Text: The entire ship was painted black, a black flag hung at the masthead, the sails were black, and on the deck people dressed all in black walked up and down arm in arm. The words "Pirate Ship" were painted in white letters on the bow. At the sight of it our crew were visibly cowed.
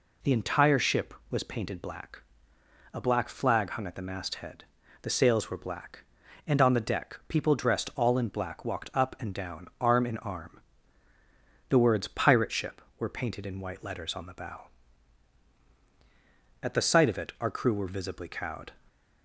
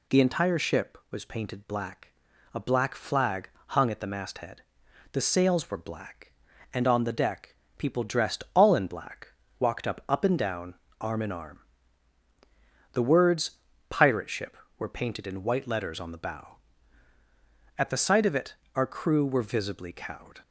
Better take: first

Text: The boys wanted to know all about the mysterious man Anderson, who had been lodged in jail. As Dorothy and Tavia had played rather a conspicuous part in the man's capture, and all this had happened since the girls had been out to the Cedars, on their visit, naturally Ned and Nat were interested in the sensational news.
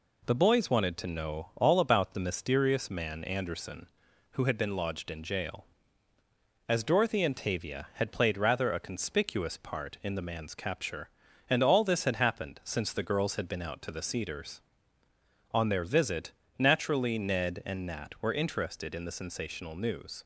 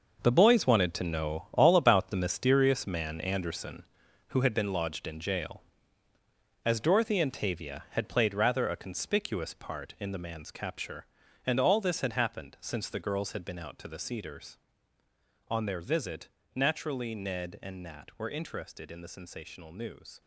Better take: first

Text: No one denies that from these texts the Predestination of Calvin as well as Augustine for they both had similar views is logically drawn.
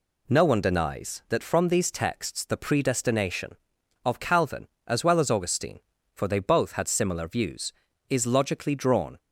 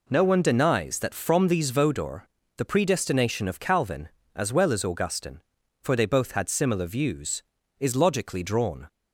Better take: first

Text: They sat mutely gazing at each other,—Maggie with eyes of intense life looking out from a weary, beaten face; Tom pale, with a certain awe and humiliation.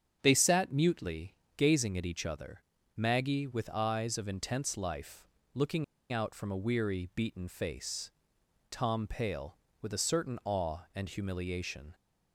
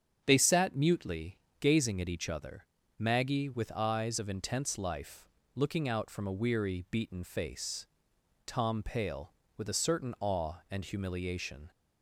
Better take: second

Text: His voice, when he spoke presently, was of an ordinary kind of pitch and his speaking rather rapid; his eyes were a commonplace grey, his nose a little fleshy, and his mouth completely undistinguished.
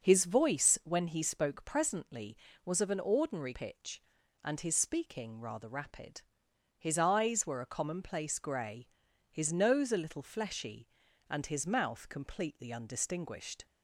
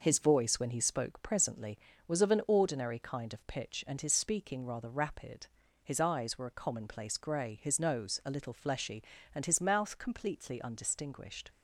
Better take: second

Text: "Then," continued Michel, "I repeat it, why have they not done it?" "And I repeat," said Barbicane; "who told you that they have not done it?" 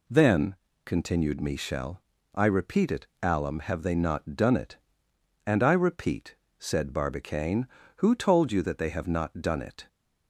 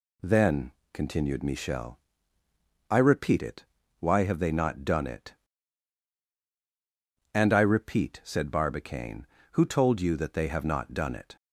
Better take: second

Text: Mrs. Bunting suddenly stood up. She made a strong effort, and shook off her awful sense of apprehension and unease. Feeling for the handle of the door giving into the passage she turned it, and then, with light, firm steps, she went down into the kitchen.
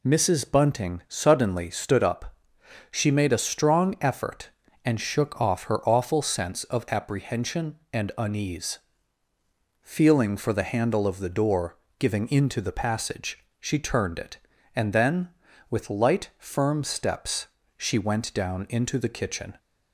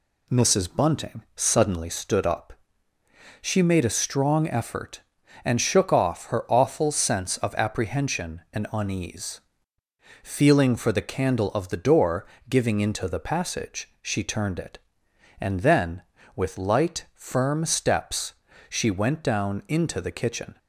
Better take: first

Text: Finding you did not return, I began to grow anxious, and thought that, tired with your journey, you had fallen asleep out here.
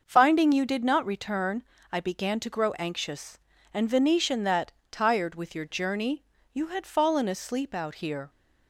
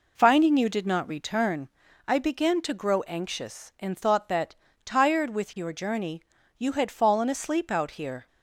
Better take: second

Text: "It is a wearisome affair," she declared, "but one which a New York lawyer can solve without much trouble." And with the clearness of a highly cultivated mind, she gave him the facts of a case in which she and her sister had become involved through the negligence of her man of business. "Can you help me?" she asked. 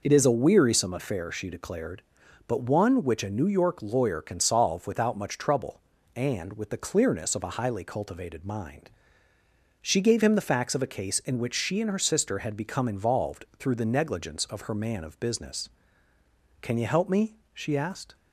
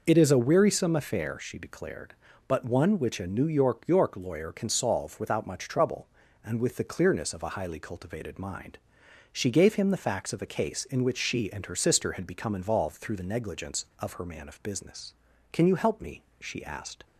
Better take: first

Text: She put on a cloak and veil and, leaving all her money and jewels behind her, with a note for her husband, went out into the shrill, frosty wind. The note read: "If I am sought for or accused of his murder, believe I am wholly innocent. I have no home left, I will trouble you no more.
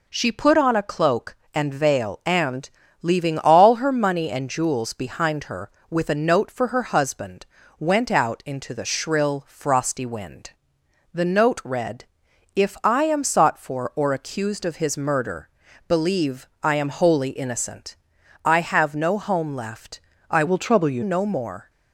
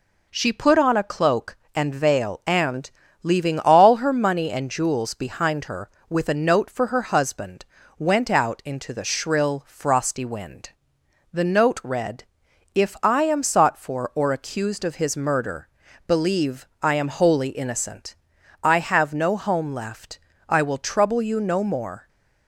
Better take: second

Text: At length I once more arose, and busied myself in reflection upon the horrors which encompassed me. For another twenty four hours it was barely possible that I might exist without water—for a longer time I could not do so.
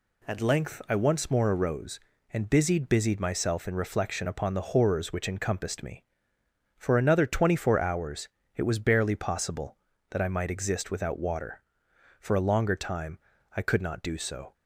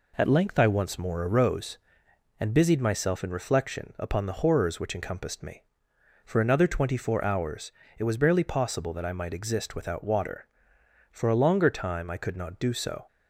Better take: second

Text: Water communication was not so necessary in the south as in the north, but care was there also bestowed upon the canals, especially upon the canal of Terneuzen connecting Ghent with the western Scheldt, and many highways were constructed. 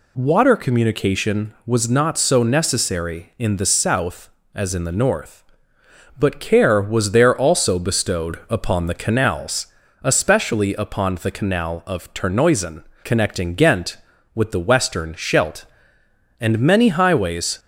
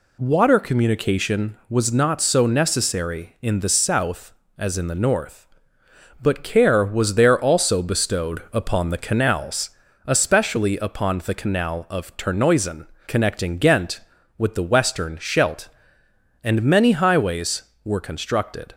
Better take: second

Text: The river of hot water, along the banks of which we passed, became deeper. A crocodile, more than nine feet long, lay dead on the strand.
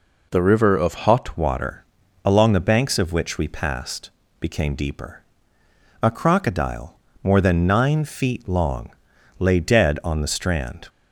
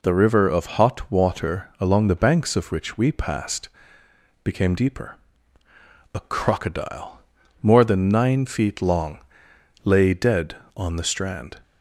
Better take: second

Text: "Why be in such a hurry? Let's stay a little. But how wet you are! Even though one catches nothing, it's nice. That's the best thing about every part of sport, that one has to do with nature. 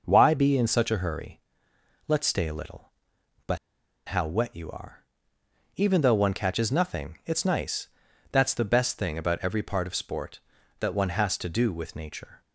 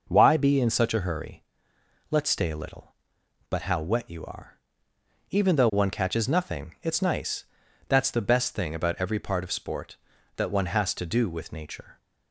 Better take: second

